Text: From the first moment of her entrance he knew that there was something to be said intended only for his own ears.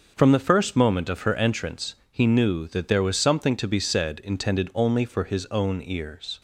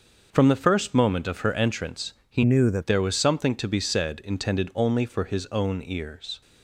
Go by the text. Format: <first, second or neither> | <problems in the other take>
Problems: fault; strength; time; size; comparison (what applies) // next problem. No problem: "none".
first | starts louder than the rest; until 1.3 s; 6.5 dB; also in the first // pauses between "entrance" and "he"; slight; at 2.1 s; 0.16 s long; slight in the first // changes voice from "knew" to "that"; from 2.4 to 2.8 s; 0.4 s long